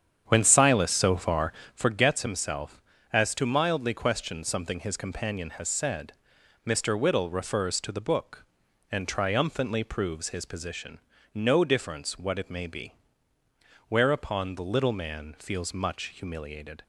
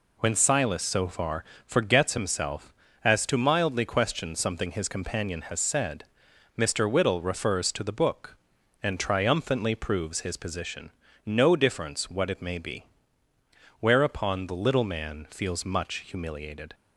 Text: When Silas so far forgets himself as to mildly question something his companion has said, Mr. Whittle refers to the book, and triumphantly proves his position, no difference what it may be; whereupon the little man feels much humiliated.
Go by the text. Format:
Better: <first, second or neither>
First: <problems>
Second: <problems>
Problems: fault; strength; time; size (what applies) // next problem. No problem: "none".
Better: second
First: starts louder than the rest; strong; until 1.9 s; 8.5 dB // pauses between "far" and "forgets"; slight; at 1.5 s; 0.22 s long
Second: pauses between "far" and "forgets"; slight; at 1.4 s; 0.22 s long